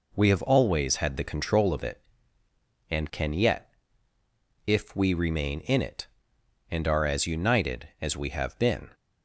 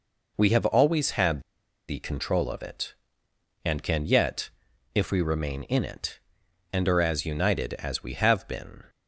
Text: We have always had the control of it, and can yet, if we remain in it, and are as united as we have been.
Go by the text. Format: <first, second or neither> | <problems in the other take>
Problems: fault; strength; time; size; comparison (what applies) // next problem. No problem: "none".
first | pauses between "had" and "the"; noticeable; at 1.3 s; 0.48 s long